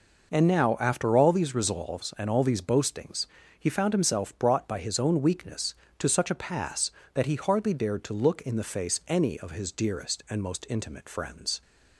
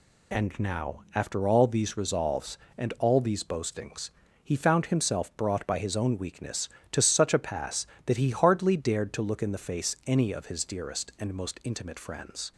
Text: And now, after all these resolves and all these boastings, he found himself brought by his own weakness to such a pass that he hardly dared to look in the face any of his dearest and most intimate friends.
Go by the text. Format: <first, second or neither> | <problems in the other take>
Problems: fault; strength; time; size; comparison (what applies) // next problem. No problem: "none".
neither | none